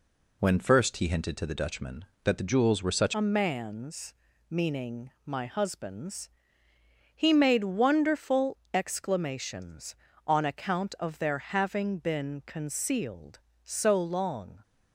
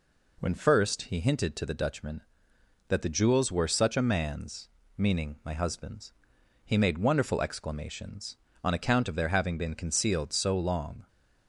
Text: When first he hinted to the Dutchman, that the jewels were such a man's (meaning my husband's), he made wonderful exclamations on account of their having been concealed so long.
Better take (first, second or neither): second